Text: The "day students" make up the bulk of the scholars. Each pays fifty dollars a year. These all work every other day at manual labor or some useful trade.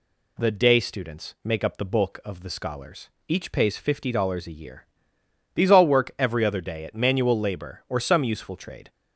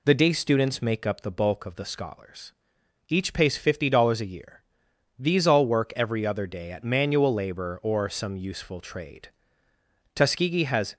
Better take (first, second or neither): first